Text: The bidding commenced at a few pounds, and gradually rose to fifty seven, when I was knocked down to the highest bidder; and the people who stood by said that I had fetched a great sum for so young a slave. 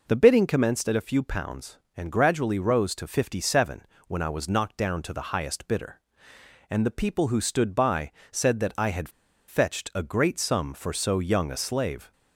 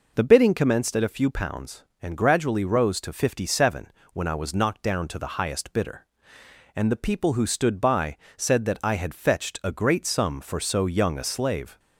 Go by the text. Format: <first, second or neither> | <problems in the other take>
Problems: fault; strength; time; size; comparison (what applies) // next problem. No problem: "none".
second | pauses between "by" and "said"; slight; at 8.1 s; 0.20 s long; slight in the second // pauses between "had" and "fetched"; at 9.0 s; 0.38 s long